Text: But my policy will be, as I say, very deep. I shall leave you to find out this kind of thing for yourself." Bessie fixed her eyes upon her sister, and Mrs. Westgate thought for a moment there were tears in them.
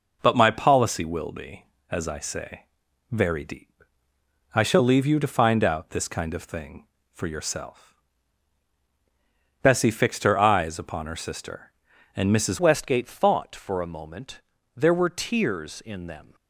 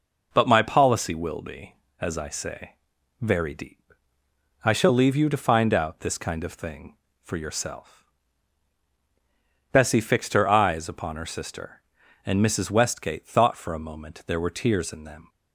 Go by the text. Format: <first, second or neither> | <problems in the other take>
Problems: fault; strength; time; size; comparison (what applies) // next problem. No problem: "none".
second | changes voice at "Westgate"; from 12.5 s on; 3.8 s long // pauses between "moment" and "there"; slight; at 14.4 s; 0.34 s long